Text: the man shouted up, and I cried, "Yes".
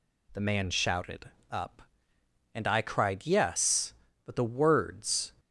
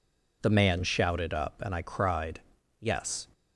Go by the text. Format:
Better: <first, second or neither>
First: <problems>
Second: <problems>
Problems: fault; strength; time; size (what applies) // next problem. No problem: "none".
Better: second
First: pauses between "shouted" and "up"; slight; at 1.3 s; 0.20 s long // goes on to say "But the words"; noticeable; from 4.2 s on; 1.0 s long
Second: none